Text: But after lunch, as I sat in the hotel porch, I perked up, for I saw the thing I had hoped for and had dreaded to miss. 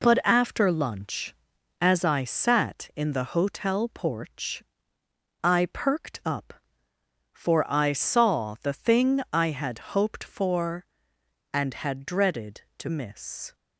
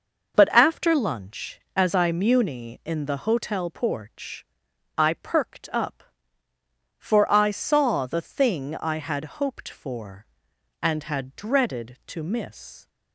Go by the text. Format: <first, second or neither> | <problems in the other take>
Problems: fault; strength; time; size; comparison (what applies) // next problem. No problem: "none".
first | says "muni" for "sat"; at 2.0 s